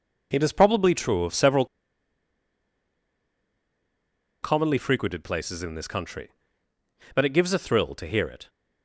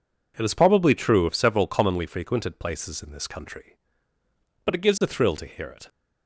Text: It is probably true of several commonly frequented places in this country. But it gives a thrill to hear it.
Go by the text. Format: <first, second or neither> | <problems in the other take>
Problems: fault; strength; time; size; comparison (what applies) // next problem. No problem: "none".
second | pauses between "several" and "commonly"; strong; at 1.6 s; 2.7 s long